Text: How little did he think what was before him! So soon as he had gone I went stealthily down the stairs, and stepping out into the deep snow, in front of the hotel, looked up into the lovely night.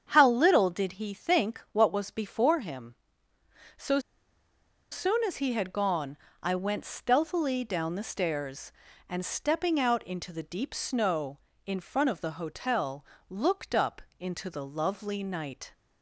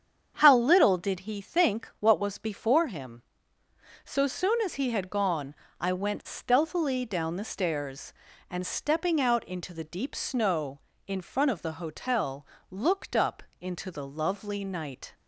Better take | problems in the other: second | starts louder than the rest; strong; until 1.1 s; 8 dB; strong in the second // pauses between "So" and "soon"; noticeable; at 3.9 s; 0.92 s long // pauses between "gone" and "I"; slight; at 6.1 s; 0.24 s long; slight in the second // pauses between "up" and "into"; slight; at 14.0 s; 0.18 s long; slight in the second

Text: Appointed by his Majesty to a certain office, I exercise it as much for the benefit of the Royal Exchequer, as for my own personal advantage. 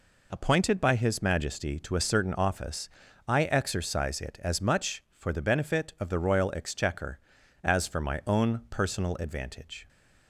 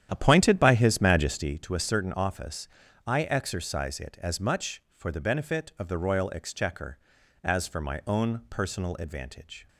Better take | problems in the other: first | starts louder than the rest; strong; until 1.6 s; 10 dB

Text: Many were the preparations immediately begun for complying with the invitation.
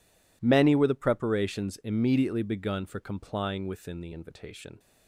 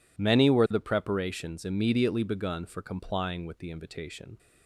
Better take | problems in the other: second | says "within" for "with"; at 3.6 s

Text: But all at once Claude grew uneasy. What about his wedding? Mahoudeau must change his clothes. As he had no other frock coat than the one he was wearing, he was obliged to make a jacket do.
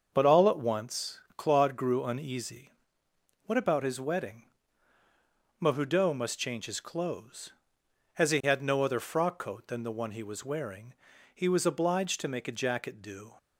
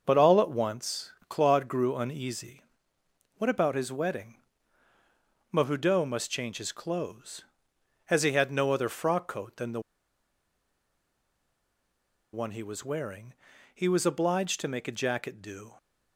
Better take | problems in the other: first | starts louder than the rest; until 1.0 s; 6.5 dB; also in the first // pauses between "once" and "Claude"; slight; at 1.1 s; 0.16 s long; slight in the first // pauses between "the" and "one"; strong; at 9.7 s; 2.5 s long

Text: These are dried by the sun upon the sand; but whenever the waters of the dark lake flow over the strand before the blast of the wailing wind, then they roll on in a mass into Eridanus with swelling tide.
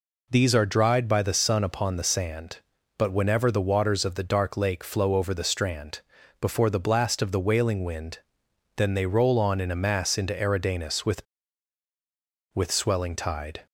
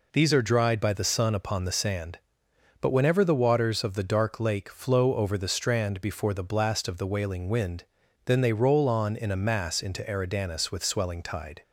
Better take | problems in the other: second | pauses between "strand" and "before"; at 5.9 s; 0.40 s long // says "with" twice; at 12.5 s

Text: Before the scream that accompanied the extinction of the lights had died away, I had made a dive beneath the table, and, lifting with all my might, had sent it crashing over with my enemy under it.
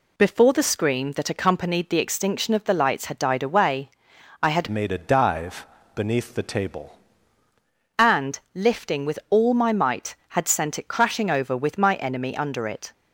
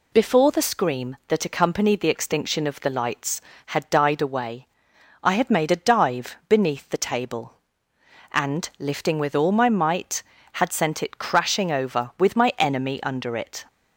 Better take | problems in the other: second | changes voice from "made" to "table"; from 4.6 to 6.9 s; 2.3 s long // pauses between "dive" and "beneath"; slight; at 5.6 s; 0.28 s long

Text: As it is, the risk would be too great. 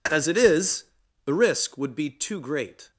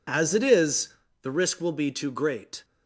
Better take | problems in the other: first | says "will" for "would"; at 1.6 s

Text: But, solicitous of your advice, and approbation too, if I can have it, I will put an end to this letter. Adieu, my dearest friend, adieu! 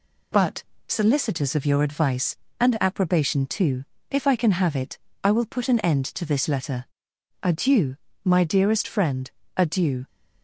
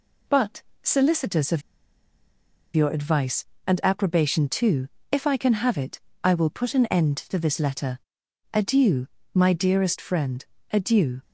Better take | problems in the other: first | pauses between "of" and "your"; at 1.6 s; 1.1 s long

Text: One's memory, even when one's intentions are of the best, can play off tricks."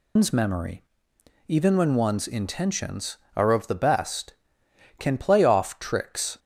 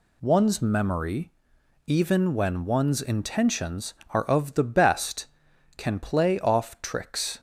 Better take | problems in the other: second | loses the start of "One's"; at 0.1 s; 125 ms

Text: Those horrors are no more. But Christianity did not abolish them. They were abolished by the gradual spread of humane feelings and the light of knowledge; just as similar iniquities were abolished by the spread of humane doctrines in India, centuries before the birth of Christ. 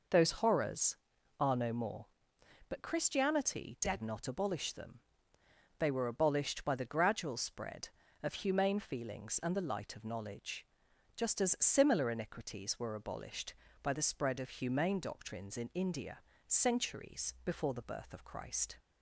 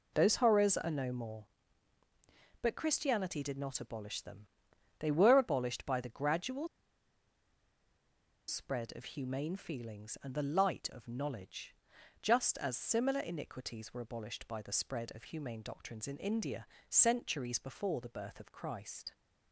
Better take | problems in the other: first | pauses between "gradual" and "spread"; strong; at 6.6 s; 1.8 s long

